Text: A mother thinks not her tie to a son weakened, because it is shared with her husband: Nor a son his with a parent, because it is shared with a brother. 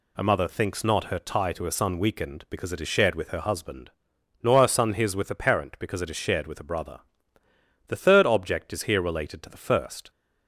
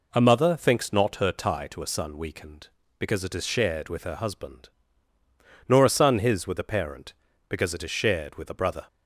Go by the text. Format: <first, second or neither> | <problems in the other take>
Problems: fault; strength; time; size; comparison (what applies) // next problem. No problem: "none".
second | goes on to say "The third object is here related to the first"; strong; from 7.8 s on; 2.2 s long